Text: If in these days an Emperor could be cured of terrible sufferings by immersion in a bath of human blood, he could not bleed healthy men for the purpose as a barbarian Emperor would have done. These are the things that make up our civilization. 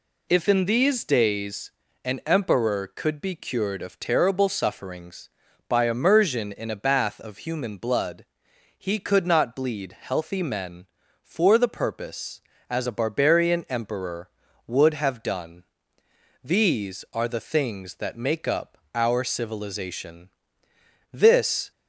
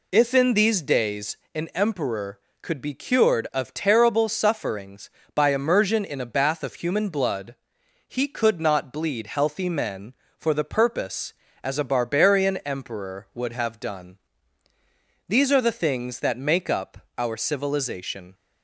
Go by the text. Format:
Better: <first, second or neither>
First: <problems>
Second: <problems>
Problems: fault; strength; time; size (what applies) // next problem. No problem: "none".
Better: second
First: pauses between "days" and "an"; slight; at 1.7 s; 0.32 s long // pauses between "up" and "our"; slight; at 18.7 s; 0.18 s long // goes on to say "This"; from 21.1 s on; 0.58 s long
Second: pauses between "days" and "an"; slight; at 1.3 s; 0.18 s long // pauses between "up" and "our"; slight; at 16.9 s; 0.18 s long